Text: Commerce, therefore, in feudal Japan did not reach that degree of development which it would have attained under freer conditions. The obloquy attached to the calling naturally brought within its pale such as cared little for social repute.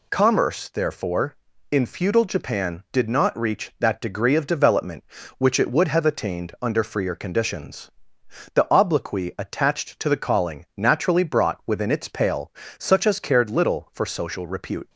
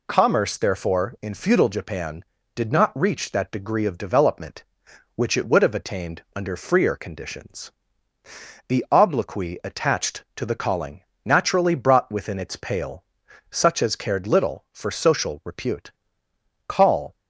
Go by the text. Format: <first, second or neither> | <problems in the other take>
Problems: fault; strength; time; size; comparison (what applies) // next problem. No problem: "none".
first | pauses between "calling" and "naturally"; slight; at 11.0 s; 0.18 s long // pauses between "pale" and "such"; at 13.0 s; 0.44 s long; slight in the first // goes on to say "Call"; slight; from 16.6 s on; 0.48 s long